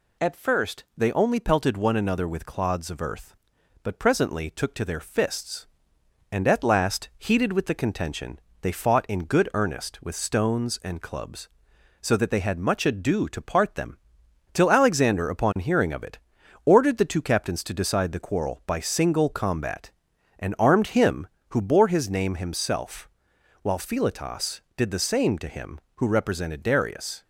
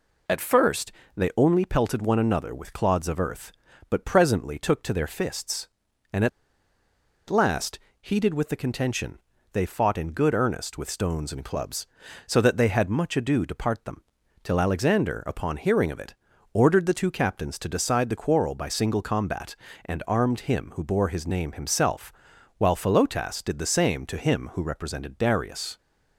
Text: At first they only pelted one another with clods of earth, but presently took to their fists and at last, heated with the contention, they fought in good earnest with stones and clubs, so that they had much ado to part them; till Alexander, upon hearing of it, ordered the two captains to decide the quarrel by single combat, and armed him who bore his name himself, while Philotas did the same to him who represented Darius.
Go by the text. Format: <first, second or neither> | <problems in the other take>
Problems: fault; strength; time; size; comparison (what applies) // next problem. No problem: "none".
first | pauses between "first" and "they"; slight; at 0.9 s; 0.24 s long // pauses between "at" and "last"; at 6.2 s; 0.99 s long